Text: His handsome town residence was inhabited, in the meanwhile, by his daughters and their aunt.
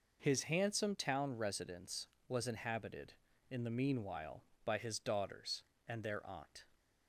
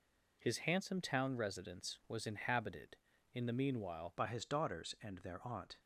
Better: first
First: none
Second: changes voice at "by"; from 4.1 s on; 1.6 s long

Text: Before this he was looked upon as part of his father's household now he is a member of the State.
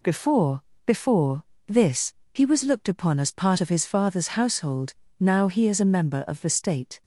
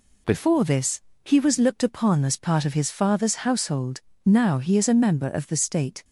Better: second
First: says "Before" twice; at 0.8 s // pauses between "this" and "he"; slight; at 2.1 s; 0.22 s long // pauses between "household" and "now"; slight; at 4.9 s; 0.26 s long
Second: pauses between "this" and "he"; slight; at 1.0 s; 0.24 s long // pauses between "household" and "now"; slight; at 4.0 s; 0.26 s long

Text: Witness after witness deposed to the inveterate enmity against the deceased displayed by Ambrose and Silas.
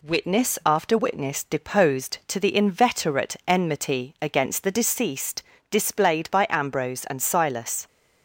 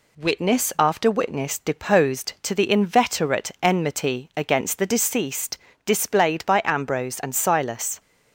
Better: neither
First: pauses between "deceased" and "displayed"; slight; at 5.4 s; 0.30 s long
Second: pauses between "deceased" and "displayed"; slight; at 5.5 s; 0.30 s long

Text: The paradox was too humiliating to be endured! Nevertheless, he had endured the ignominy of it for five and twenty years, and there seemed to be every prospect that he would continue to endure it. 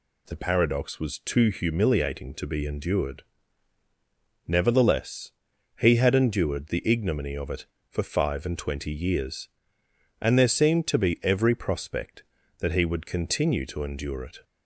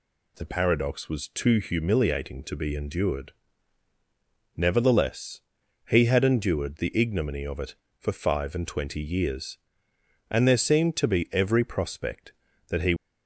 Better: first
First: none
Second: stops before "would continue to endure it"; at 12.9 s

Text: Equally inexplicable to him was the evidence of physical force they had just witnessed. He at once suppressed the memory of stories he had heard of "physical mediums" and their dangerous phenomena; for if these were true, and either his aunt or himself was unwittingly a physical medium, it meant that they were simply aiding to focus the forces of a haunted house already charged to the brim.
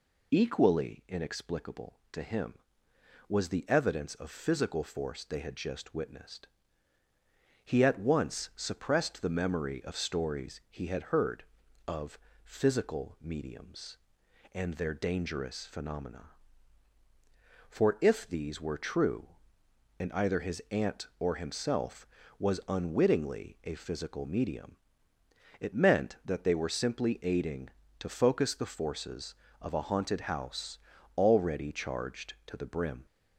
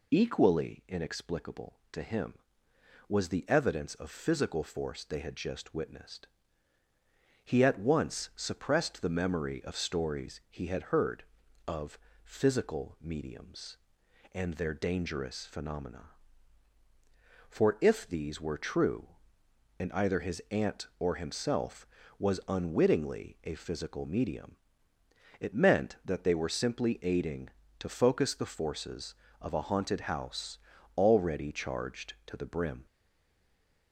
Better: first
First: pauses between "of" and "physical"; slight; at 12.1 s; 0.26 s long // pauses between "house" and "already"; at 30.7 s; 0.40 s long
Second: pauses between "of" and "physical"; slight; at 11.9 s; 0.26 s long // pauses between "house" and "already"; at 30.5 s; 0.40 s long // stays silent after the last word; from 32.8 s on; 1.1 s long

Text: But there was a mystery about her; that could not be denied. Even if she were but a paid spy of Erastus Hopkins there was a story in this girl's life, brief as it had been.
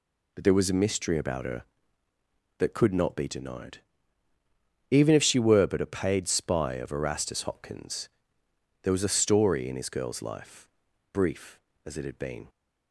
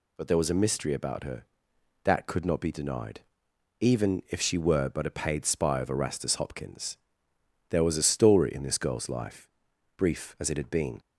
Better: second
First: pauses between "Hopkins" and "there"; noticeable; at 8.0 s; 0.76 s long // says "his" for "this"; at 9.7 s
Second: pauses between "Hopkins" and "there"; noticeable; at 6.9 s; 0.72 s long

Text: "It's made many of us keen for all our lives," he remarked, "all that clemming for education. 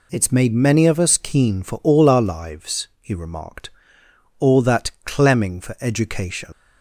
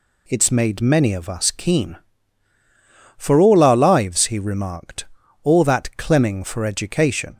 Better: second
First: leaves "education" unfinished; at 6.5 s; 120 ms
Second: none

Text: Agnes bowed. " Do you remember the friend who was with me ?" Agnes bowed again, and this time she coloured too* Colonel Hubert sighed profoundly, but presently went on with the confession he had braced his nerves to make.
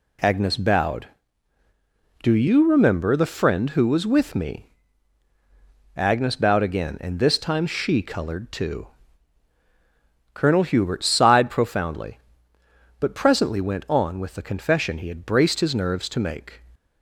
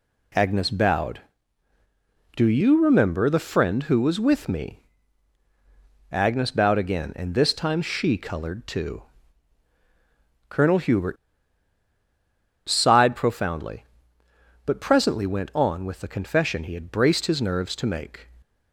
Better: first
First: pauses between "too" and "Colonel"; strong; at 8.8 s; 1.4 s long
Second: pauses between "too" and "Colonel"; strong; at 9.0 s; 1.4 s long // pauses between "Hubert" and "sighed"; strong; at 11.1 s; 1.5 s long

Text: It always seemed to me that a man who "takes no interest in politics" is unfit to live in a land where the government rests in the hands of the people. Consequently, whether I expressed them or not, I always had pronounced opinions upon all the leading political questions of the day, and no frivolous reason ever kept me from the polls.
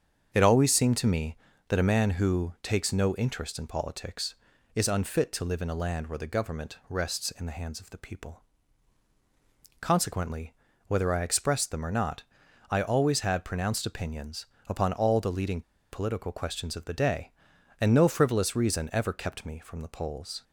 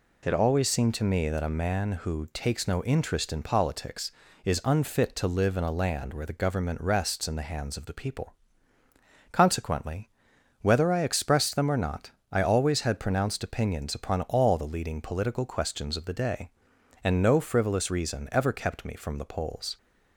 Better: second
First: starts louder than the rest; strong; until 1.3 s; 7.5 dB // pauses between "opinions" and "upon"; slight; at 14.4 s; 0.20 s long // pauses between "leading" and "political"; slight; at 15.6 s; 0.31 s long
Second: none

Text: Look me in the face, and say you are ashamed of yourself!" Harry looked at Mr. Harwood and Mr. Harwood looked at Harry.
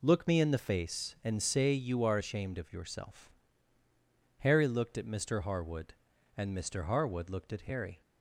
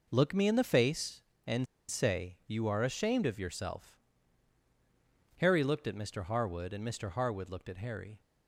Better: first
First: none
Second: pauses between "and" and "say"; slight; at 1.6 s; 0.24 s long

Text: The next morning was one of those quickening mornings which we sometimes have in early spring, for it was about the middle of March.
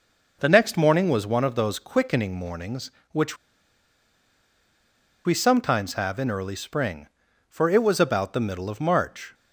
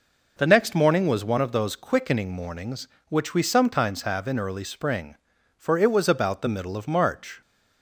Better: second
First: pauses between "which" and "we"; strong; at 3.3 s; 1.8 s long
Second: none

